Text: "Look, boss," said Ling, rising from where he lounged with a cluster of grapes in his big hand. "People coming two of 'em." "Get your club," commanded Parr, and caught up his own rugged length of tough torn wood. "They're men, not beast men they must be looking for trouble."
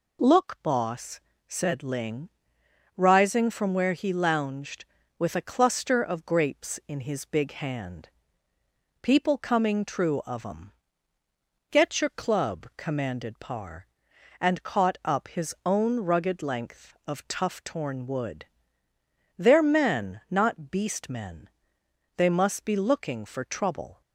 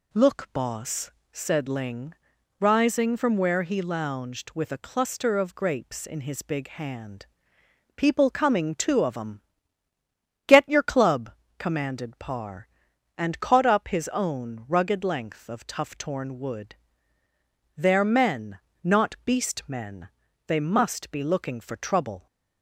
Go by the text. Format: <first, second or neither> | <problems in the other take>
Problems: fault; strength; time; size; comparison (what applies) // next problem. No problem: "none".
second | says "true" for "two"; at 9.8 s // pauses between "men" and "they"; noticeable; at 21.4 s; 0.68 s long; also in the second